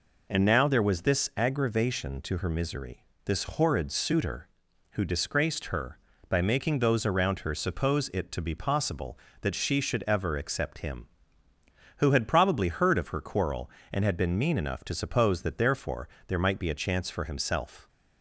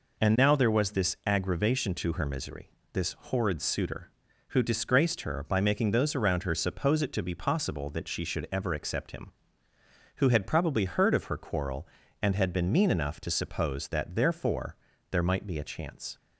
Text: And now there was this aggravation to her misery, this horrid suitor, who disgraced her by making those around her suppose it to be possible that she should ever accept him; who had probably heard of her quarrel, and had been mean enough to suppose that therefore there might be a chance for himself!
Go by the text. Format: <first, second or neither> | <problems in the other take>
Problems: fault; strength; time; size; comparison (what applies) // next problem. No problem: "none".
first | pauses between "therefore" and "there"; slight; at 14.7 s; 0.36 s long; slight in the first // stops before "for himself"; at 16.1 s